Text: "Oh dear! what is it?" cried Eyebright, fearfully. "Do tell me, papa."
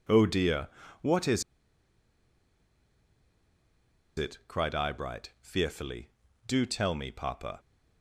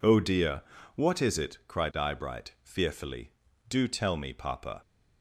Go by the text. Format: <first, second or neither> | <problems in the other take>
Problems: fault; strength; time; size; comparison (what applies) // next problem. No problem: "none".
second | pauses between "is" and "it"; strong; at 1.4 s; 2.7 s long